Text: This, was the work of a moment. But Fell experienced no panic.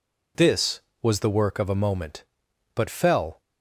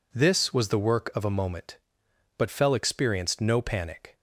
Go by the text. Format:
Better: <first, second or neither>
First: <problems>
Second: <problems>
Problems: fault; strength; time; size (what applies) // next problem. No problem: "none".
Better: second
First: stops before "experienced no panic"; at 3.3 s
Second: none